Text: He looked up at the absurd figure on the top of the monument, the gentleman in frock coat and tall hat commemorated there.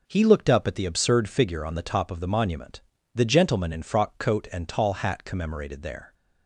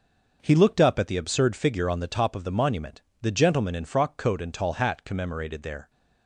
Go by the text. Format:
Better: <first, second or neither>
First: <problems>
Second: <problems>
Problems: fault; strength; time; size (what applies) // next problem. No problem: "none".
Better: neither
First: none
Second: none